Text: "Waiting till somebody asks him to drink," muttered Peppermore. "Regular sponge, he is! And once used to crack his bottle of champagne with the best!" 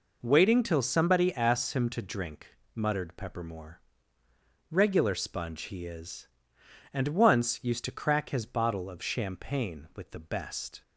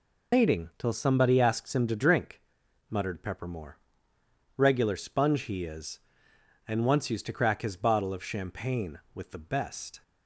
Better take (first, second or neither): first